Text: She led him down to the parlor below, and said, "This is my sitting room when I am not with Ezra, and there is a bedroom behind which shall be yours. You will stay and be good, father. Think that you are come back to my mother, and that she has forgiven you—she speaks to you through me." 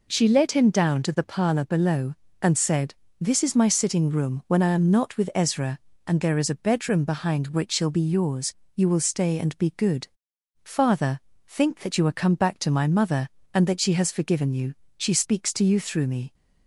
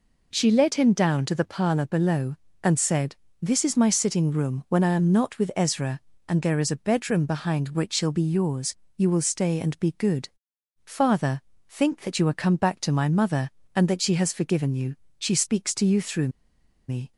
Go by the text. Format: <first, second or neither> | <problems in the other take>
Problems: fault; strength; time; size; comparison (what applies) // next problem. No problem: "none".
first | pauses between "through" and "me"; noticeable; at 16.2 s; 0.59 s long